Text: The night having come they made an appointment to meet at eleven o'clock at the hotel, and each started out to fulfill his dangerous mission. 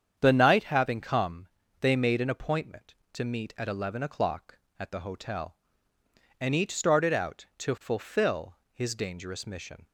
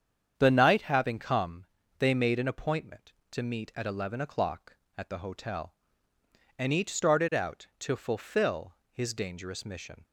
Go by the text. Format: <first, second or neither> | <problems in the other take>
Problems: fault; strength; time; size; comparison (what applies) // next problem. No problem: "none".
neither | starts louder than the rest; strong; the same in both // pauses between "come" and "they"; slight; the same in both // pauses between "fulfill" and "his"; slight; the same in both